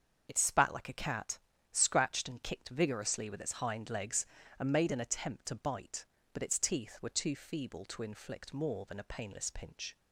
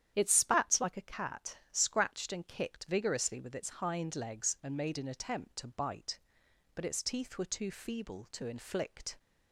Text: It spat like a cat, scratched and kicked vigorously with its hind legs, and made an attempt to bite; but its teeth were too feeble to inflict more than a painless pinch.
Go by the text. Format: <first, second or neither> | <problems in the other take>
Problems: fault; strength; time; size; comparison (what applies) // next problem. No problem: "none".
first | starts louder than the rest; strong; until 1.1 s; 10 dB; also in the first // stops before "more than a painless pinch"; at 9.1 s